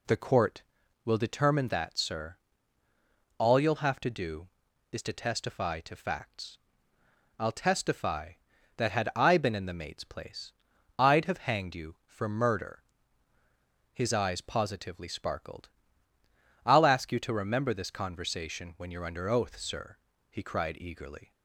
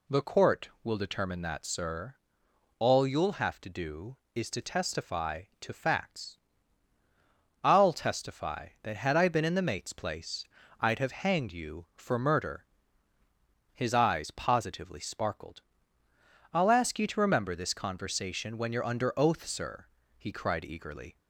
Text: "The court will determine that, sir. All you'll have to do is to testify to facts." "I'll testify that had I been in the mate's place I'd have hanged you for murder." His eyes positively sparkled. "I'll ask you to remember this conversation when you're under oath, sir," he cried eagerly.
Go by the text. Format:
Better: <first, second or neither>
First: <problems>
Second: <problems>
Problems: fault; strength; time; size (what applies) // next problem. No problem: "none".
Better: neither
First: pauses between "place" and "I'd"; at 10.5 s; 0.44 s long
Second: pauses between "place" and "I'd"; slight; at 10.4 s; 0.34 s long